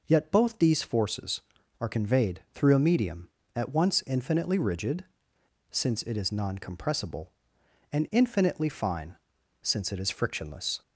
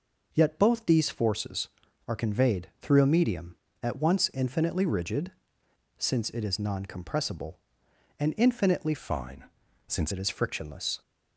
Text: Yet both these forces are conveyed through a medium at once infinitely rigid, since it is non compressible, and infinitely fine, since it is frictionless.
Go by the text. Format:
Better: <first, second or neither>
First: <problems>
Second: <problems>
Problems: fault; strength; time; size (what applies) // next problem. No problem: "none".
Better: first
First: none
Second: changes voice from "fine" to "since"; from 8.9 to 10.1 s; 1.2 s long